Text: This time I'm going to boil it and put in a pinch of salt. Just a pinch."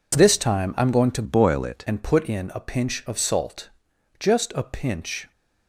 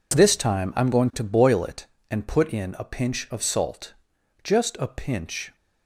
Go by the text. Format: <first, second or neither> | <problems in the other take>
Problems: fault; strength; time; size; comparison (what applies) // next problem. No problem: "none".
second | changes voice from "boil" to "it"; from 1.2 to 1.8 s; 0.6 s long